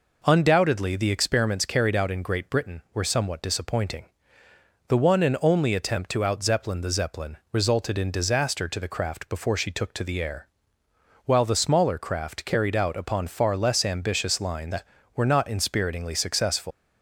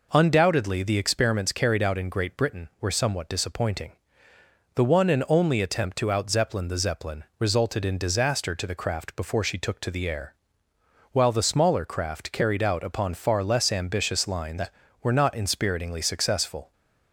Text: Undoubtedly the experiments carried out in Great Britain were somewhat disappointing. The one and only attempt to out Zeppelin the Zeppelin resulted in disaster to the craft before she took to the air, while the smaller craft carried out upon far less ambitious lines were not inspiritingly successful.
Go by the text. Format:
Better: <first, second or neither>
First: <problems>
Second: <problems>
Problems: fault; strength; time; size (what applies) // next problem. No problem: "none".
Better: second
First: leaves "successful" unfinished; at 16.7 s; 140 ms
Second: none